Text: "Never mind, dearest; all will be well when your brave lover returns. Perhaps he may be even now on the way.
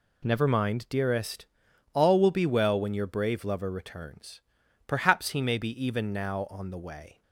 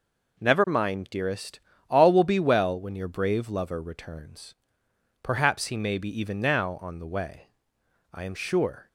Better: first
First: none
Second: goes on to say "I am sure"; noticeable; from 8.1 s on; 0.74 s long

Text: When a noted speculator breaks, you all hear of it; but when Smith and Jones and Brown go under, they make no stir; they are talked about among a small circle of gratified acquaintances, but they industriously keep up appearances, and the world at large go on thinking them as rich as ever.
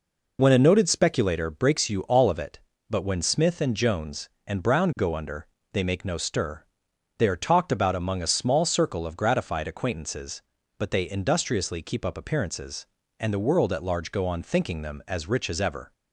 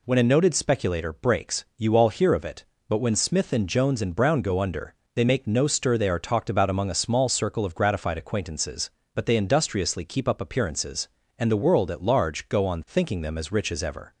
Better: second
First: skips "hear"; at 2.3 s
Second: none

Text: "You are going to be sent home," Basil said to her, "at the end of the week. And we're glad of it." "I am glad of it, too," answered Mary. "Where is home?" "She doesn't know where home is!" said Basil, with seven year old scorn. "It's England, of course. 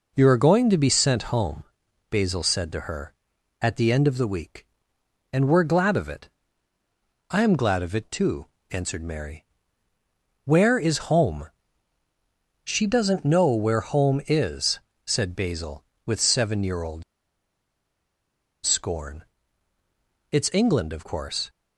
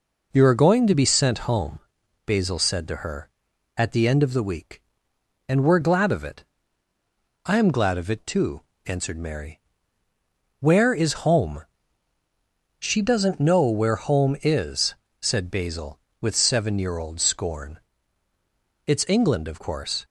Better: second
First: pauses between "old" and "scorn"; strong; at 17.0 s; 1.6 s long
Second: none

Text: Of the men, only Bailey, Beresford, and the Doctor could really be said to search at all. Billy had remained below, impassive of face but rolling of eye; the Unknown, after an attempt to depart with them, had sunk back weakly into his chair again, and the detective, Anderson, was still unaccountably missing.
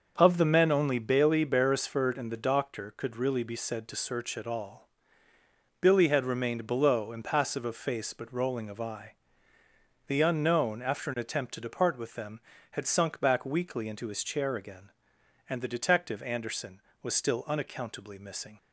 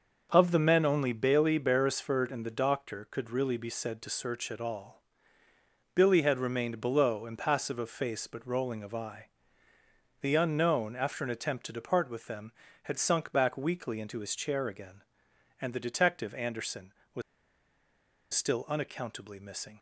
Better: first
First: starts louder than the rest; until 1.1 s; 6.5 dB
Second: starts louder than the rest; until 1.3 s; 6.5 dB // pauses between "was" and "still"; at 17.2 s; 1.1 s long

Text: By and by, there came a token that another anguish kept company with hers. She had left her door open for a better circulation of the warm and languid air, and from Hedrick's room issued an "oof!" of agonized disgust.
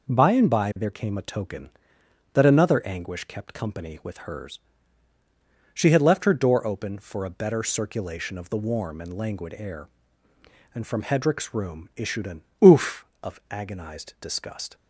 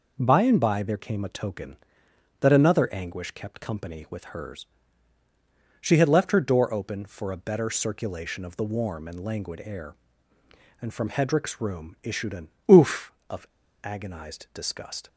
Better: first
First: pauses between "an" and "oof"; slight; at 12.4 s; 0.20 s long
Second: pauses between "an" and "oof"; slight; at 12.4 s; 0.20 s long // pauses between "of" and "agonized"; at 13.4 s; 0.38 s long

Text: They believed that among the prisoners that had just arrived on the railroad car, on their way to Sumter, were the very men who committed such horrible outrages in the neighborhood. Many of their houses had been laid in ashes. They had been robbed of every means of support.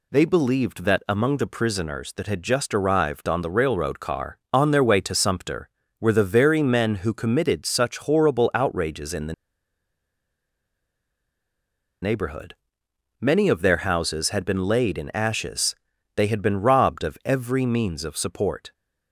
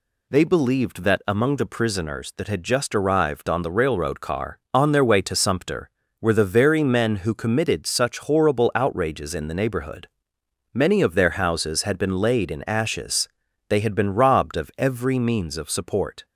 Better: second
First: pauses between "the" and "neighborhood"; strong; at 9.3 s; 2.6 s long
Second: none

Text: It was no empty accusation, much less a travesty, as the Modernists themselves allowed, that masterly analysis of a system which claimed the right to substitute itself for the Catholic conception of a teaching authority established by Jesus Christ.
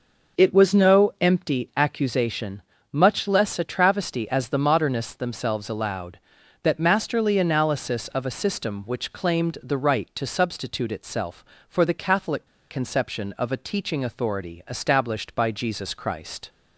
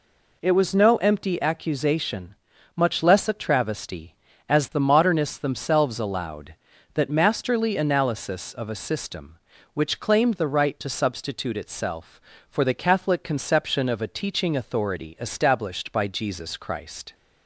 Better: second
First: pauses between "Catholic" and "conception"; slight; at 12.4 s; 0.21 s long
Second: none

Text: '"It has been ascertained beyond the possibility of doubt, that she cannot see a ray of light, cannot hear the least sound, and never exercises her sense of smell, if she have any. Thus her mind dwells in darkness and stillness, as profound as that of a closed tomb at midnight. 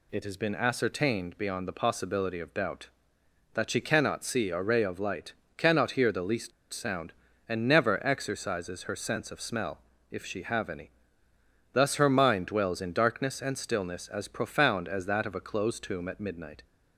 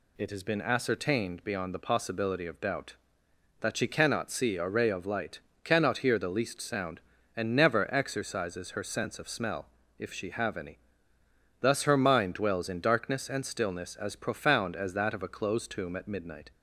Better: second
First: pauses between "least" and "sound"; slight; at 6.5 s; 0.22 s long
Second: none

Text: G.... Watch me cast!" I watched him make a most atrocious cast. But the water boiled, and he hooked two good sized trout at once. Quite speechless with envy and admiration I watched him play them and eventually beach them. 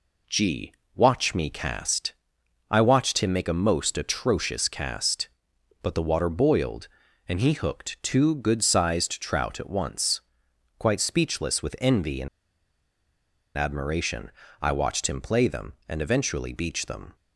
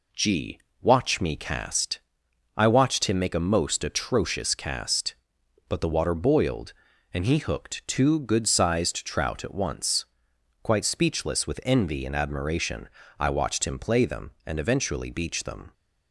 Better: second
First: pauses between "and" and "admiration"; strong; at 12.2 s; 1.2 s long // pauses between "admiration" and "I"; slight; at 14.3 s; 0.30 s long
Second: pauses between "admiration" and "I"; slight; at 12.8 s; 0.30 s long

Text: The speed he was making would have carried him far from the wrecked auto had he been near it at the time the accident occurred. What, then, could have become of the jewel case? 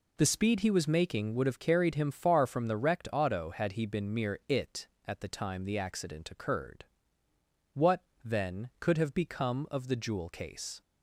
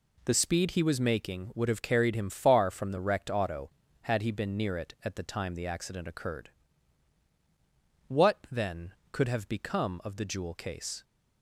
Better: second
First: says "mere" for "near"; at 4.1 s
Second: none

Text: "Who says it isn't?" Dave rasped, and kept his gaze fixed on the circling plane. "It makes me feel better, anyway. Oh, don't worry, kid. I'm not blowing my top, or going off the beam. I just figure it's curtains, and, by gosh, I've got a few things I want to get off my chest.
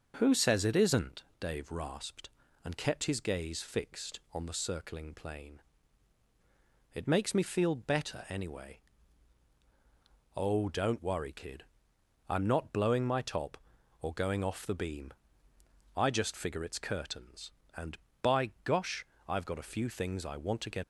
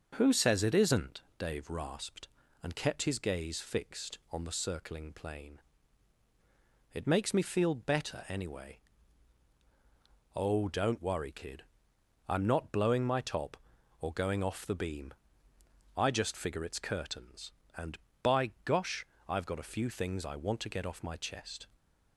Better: second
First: starts louder than the rest; until 1.1 s; 6.5 dB // stops before "off my chest"; at 20.8 s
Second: starts louder than the rest; until 1.1 s; 6.5 dB

